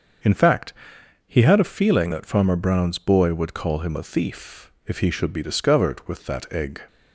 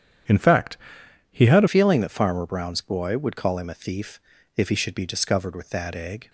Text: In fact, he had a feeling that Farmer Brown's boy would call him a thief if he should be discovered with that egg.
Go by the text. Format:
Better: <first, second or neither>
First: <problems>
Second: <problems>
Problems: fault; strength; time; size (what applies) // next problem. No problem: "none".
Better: first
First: starts louder than the rest; until 1.8 s; 6.5 dB // pauses between "thief" and "if"; slight; at 4.7 s; 0.16 s long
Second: starts louder than the rest; strong; until 1.8 s; 9 dB // changes voice at "feeling"; from 1.6 s on; 4.6 s long // pauses between "thief" and "if"; slight; at 4.1 s; 0.36 s long